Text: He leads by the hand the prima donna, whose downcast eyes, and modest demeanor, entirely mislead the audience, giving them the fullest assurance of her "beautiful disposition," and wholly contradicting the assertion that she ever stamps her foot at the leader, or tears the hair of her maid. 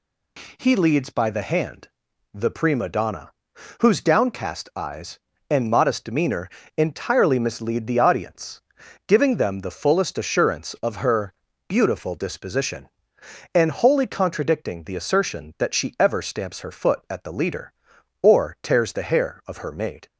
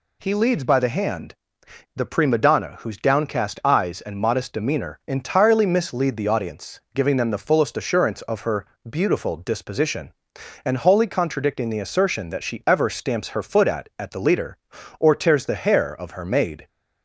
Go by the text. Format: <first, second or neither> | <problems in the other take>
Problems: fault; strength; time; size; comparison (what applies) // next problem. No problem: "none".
first | pauses between "hand" and "the"; noticeable; at 1.3 s; 0.62 s long; also in the first // pauses between "her" and "beautiful"; slight; at 8.6 s; 0.24 s long; slight in the first // says "at" twice; at 13.9 s